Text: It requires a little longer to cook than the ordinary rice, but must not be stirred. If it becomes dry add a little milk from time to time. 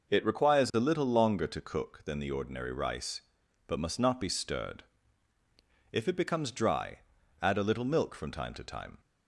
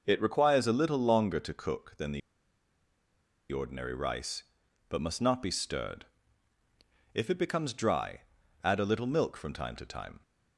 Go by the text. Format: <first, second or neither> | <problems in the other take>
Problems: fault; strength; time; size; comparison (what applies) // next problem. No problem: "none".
first | pauses between "the" and "ordinary"; strong; at 2.2 s; 1.3 s long // pauses between "dry" and "add"; at 8.2 s; 0.42 s long; also in the first